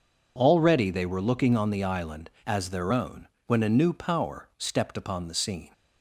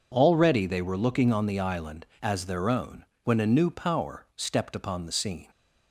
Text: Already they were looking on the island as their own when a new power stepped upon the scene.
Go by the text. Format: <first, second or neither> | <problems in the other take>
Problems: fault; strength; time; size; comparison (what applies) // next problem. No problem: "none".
neither | pauses between "own" and "when"; slight; the same in both